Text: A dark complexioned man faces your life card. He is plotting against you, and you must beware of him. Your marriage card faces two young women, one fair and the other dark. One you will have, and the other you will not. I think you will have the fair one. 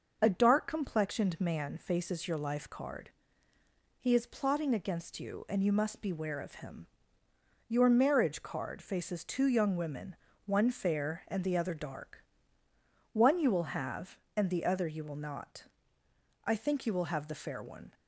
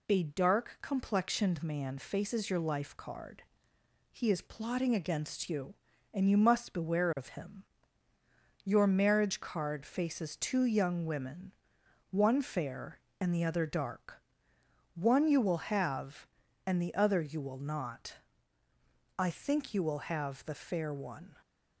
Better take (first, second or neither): neither